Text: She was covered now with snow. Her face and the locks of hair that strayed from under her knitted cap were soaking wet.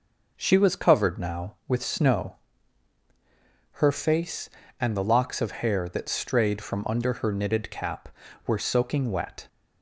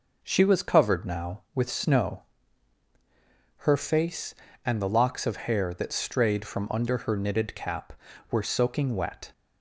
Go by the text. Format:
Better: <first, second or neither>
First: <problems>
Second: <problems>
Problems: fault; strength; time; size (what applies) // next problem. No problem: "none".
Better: neither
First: starts louder than the rest; noticeable; until 1.3 s; 6 dB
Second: starts louder than the rest; noticeable; until 1.2 s; 6 dB